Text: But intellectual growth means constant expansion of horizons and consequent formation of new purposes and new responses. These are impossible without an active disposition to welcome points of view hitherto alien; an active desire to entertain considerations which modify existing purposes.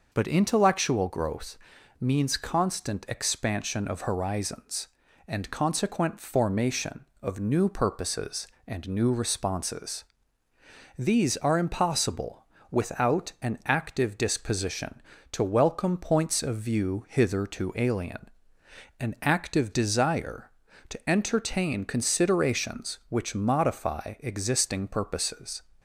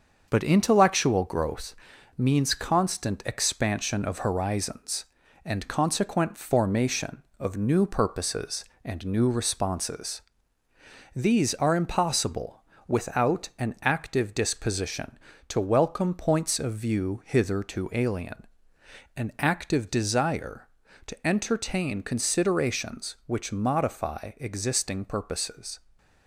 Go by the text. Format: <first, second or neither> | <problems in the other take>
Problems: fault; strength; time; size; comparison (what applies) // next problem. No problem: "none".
first | gets quieter; noticeable; throughout; 5 dB // pauses between "growth" and "means"; at 1.7 s; 0.44 s long; also in the first // pauses between "impossible" and "without"; slight; at 12.6 s; 0.25 s long; slight in the first